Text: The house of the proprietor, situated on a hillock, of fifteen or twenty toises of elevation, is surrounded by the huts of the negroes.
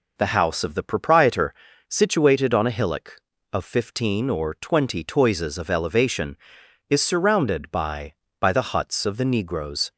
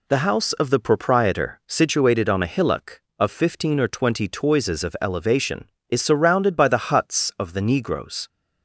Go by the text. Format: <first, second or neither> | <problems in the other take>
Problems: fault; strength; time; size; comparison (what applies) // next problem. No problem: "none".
second | says "by" twice; at 8.4 s